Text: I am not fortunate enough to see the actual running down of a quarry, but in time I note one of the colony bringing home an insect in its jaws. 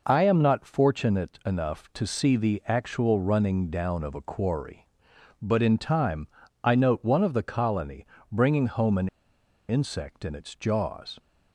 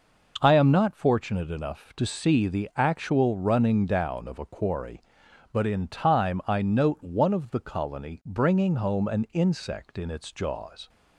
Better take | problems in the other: second | pauses between "time" and "I"; slight; at 6.2 s; 0.36 s long // pauses between "colony" and "bringing"; slight; at 8.0 s; 0.24 s long // pauses between "an" and "insect"; noticeable; at 9.0 s; 0.61 s long

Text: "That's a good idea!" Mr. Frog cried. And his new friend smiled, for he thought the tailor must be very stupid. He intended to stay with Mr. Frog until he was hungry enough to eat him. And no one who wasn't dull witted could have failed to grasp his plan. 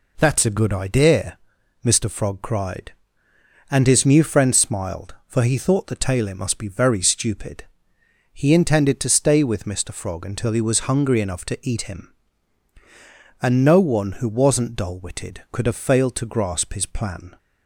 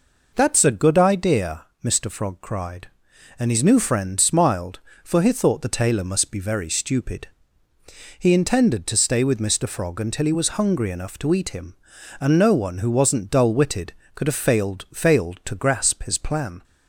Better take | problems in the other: first | says "failed" twice; at 14.9 s

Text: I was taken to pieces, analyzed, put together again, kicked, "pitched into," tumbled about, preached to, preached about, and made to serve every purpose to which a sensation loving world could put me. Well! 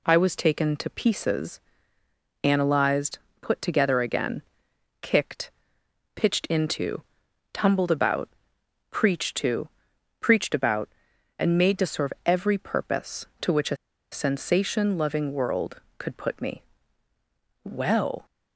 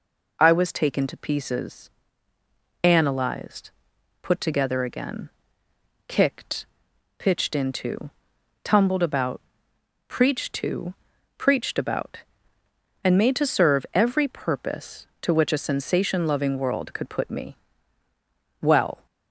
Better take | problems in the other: second | pauses between "a" and "sensation"; slight; at 13.7 s; 0.35 s long

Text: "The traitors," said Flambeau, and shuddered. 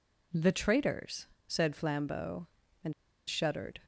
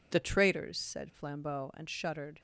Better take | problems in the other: second | pauses between "and" and "shuddered"; slight; at 2.9 s; 0.35 s long

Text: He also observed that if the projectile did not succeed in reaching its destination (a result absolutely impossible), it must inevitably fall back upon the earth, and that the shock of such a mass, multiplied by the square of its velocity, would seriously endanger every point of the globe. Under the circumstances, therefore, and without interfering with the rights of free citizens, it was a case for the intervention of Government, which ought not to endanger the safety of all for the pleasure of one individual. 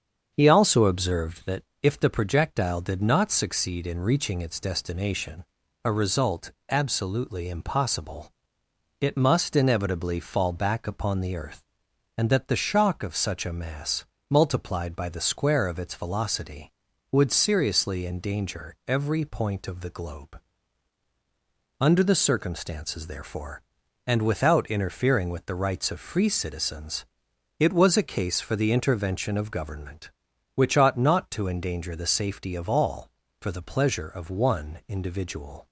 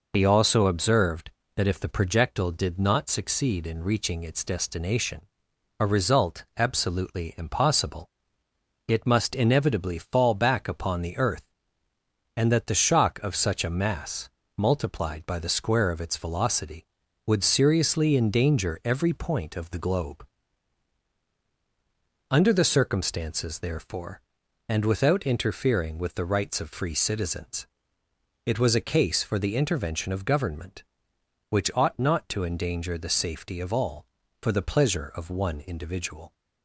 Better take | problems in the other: second | starts louder than the rest; until 1.3 s; 7 dB // pauses between "that" and "if"; slight; at 1.6 s; 0.20 s long // pauses between "result" and "absolutely"; slight; at 6.5 s; 0.18 s long

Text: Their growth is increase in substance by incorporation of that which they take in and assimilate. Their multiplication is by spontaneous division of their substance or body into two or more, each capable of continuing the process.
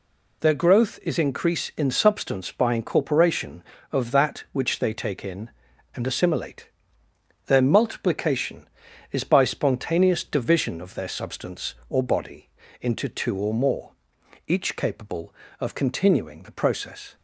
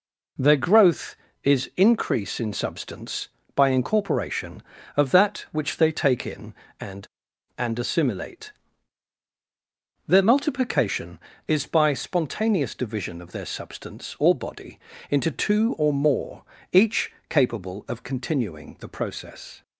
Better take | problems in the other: first | says "and" twice; at 7.5 s // pauses between "body" and "into"; slight; at 14.7 s; 0.32 s long; slight in the first // pauses between "each" and "capable"; slight; at 17.1 s; 0.16 s long

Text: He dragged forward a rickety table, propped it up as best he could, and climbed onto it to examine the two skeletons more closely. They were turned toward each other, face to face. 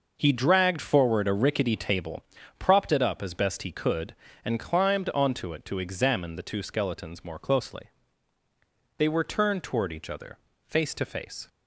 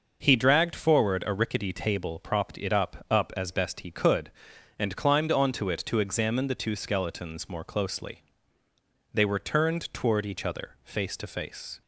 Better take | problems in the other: first | says "up" twice; at 3.0 s

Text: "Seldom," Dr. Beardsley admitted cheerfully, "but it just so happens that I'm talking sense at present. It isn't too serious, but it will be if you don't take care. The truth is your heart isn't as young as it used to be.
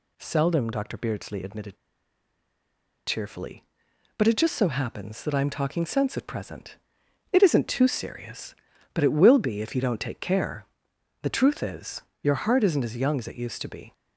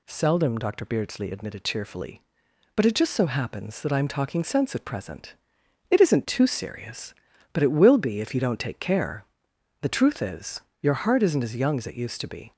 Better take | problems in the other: second | pauses between "admitted" and "cheerfully"; strong; at 1.7 s; 1.3 s long // pauses between "is" and "your"; slight; at 12.0 s; 0.22 s long; slight in the second

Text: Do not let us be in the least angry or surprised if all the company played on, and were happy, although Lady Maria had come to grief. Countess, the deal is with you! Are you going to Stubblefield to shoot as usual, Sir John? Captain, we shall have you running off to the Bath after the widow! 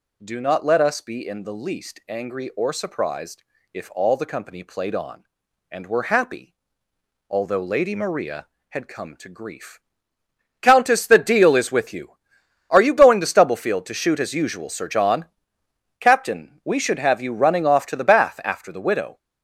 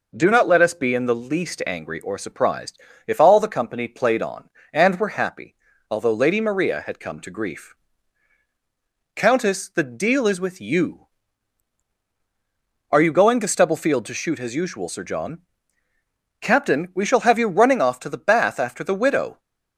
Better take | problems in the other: second | pauses between "surprised" and "if"; slight; at 3.4 s; 0.32 s long; slight in the second // says "should" for "shall"; at 16.8 s

